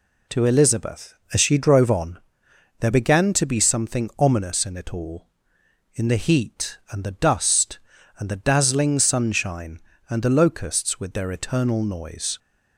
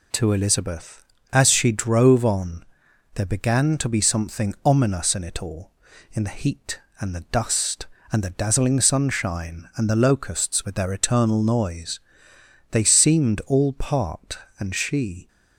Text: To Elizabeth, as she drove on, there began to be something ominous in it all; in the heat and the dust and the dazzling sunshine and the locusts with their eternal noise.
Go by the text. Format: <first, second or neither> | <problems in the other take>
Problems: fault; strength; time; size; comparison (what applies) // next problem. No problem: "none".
first | goes on to say "They seemed all part and she"; strong; from 12.7 s on; 2.5 s long